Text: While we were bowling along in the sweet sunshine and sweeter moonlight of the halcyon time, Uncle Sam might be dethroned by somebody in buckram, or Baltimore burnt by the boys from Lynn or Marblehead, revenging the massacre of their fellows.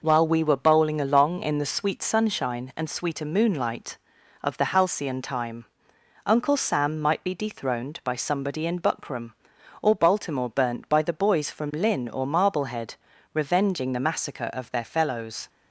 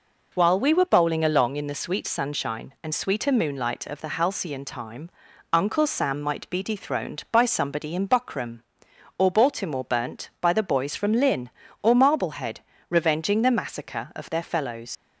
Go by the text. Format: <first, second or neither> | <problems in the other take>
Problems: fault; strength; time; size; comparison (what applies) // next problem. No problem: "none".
first | leaves "fellows" unfinished; at 14.9 s; 90 ms